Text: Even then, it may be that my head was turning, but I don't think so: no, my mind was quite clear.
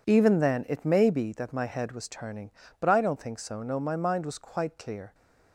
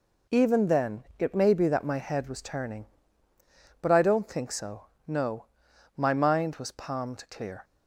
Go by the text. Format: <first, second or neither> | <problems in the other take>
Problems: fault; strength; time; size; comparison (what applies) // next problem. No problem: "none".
first | says "palmed" for "quite"; at 6.6 s